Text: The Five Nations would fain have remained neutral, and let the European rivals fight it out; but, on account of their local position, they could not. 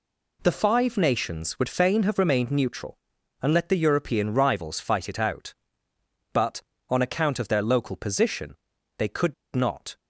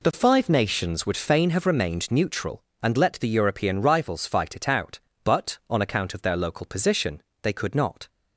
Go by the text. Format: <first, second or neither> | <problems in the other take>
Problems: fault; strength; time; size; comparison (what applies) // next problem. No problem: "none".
second | pauses between "could" and "not"; slight; at 9.3 s; 0.21 s long